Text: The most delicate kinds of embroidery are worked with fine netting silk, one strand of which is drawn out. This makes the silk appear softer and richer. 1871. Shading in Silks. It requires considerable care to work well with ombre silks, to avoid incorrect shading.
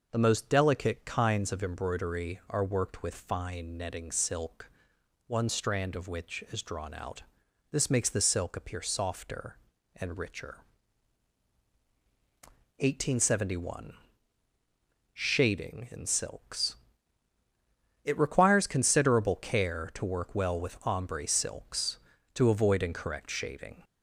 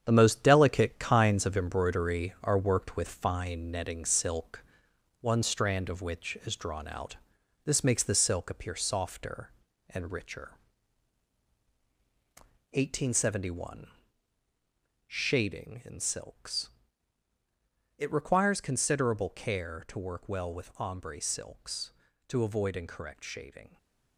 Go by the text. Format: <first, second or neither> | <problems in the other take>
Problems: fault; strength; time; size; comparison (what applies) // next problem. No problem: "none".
first | gets quieter; strong; throughout; 8 dB // stays silent after the last word; slight; from 23.6 s on; 0.5 s long